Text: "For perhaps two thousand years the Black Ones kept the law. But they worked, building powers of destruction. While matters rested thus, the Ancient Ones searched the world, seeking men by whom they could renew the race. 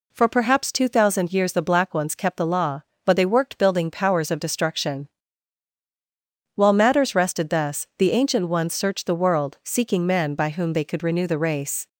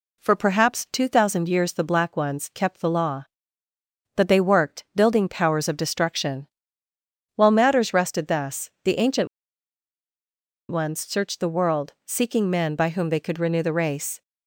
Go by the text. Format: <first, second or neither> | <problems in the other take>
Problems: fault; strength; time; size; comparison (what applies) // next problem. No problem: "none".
first | pauses between "Ancient" and "Ones"; strong; at 9.2 s; 1.4 s long